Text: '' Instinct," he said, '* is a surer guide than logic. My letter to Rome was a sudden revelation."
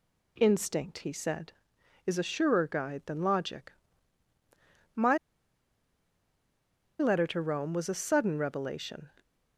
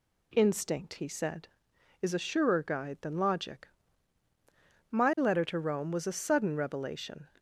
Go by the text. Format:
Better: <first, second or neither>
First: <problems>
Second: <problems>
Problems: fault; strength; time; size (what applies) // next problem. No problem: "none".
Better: second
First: pauses between "My" and "letter"; strong; at 5.1 s; 1.8 s long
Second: none